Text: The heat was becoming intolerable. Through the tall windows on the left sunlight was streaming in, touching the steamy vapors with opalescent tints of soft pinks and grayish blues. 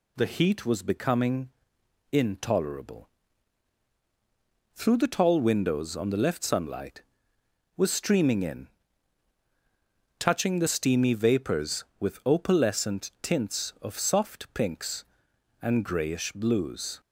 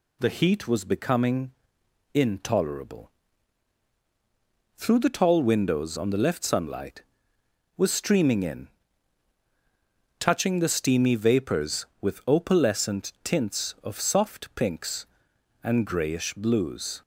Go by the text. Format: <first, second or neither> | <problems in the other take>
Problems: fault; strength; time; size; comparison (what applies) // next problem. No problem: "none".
neither | pauses between "becoming" and "intolerable"; noticeable; the same in both